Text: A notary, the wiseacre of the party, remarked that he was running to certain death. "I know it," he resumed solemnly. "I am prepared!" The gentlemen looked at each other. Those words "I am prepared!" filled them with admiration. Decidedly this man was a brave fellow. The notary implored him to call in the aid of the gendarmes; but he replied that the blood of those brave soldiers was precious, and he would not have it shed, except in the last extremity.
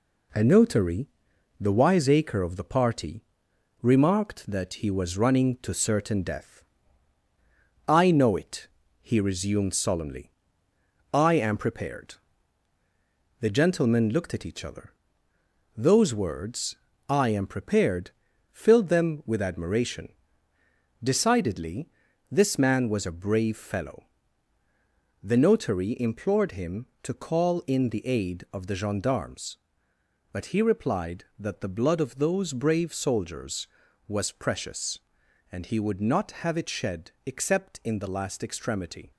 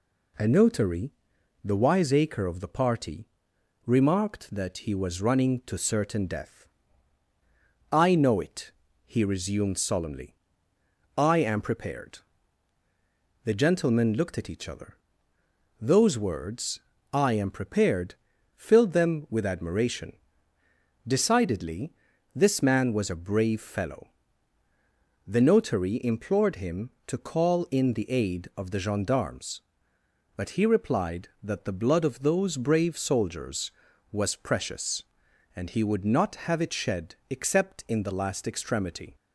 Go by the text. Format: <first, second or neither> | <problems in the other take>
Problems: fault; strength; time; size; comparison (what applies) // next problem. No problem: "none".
second | gets quieter; noticeable; throughout; 4.5 dB // pauses between "words" and "I"; slight; at 16.7 s; 0.34 s long; slight in the second // pauses between "Decidedly" and "this"; at 21.8 s; 0.40 s long; also in the second